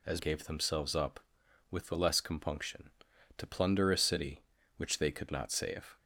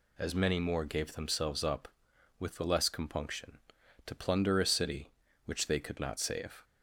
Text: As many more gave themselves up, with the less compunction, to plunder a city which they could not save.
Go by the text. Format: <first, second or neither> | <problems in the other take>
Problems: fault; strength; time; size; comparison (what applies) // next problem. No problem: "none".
second | skips "many more"; at 0.1 s